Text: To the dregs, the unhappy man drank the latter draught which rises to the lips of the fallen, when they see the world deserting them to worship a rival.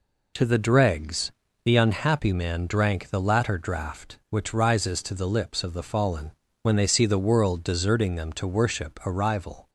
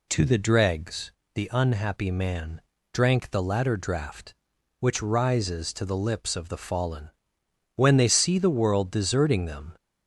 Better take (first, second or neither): first